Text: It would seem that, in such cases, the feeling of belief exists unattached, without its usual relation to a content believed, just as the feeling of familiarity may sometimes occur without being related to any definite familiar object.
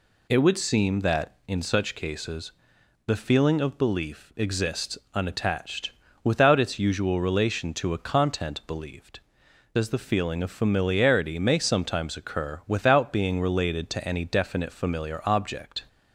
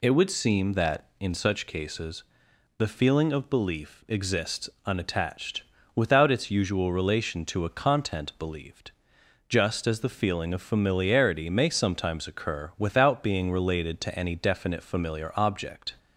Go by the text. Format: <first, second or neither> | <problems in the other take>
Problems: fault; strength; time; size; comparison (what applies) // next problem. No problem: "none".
second | pauses between "exists" and "unattached"; slight; at 4.9 s; 0.16 s long; slight in the second // skips "just"; at 9.4 s